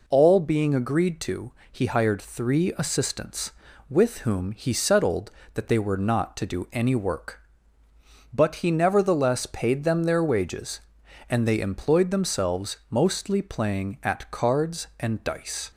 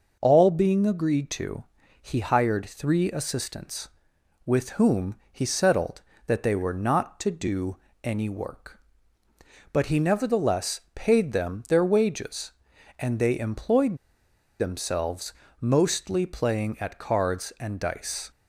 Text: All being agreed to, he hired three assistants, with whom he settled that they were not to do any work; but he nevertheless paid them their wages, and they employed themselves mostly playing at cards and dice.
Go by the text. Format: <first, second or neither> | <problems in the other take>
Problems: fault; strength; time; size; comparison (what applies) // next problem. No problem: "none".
first | pauses between "whom" and "he"; slight; at 5.1 s; 0.18 s long // pauses between "do" and "any"; slight; at 7.7 s; 0.26 s long // pauses between "nevertheless" and "paid"; slight; at 10.7 s; 0.16 s long // pauses between "employed" and "themselves"; noticeable; at 13.9 s; 0.63 s long // pauses between "themselves" and "mostly"; slight; at 15.3 s; 0.26 s long